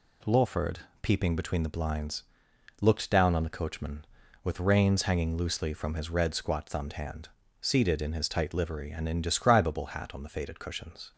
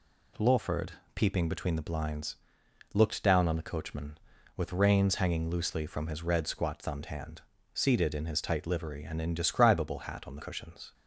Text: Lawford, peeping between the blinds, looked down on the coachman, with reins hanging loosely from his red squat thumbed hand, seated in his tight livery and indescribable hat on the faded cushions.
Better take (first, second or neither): first